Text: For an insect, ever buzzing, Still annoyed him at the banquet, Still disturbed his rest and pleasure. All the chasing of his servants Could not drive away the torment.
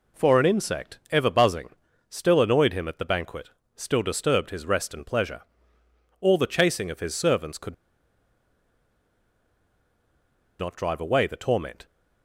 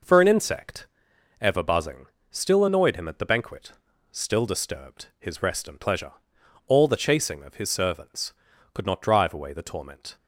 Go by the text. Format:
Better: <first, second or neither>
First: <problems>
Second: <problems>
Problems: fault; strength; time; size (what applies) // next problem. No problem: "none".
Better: second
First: pauses between "Could" and "not"; strong; at 7.7 s; 2.8 s long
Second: none